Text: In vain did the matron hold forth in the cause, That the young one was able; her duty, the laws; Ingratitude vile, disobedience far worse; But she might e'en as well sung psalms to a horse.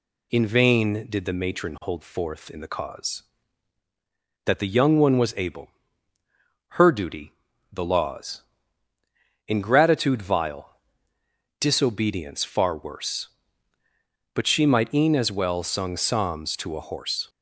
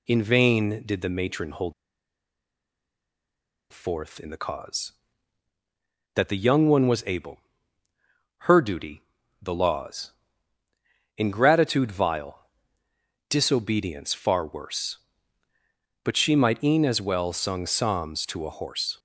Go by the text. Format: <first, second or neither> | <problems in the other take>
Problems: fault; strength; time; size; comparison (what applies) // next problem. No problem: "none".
first | pauses between "hold" and "forth"; strong; at 1.7 s; 1.9 s long